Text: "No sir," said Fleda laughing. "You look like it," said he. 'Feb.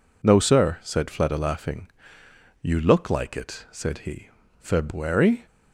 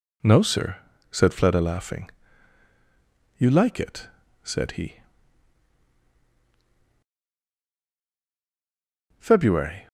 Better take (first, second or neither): first